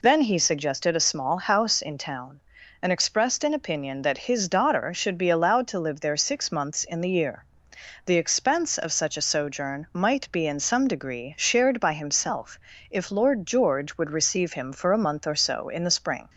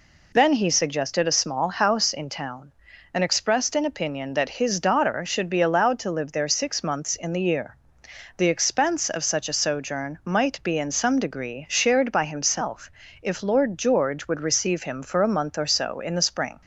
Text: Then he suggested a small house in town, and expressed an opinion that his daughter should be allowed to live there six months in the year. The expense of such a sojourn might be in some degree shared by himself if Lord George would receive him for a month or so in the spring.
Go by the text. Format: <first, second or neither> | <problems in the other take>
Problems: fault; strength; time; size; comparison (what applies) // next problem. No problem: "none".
neither | pauses between "himself" and "if"; slight; the same in both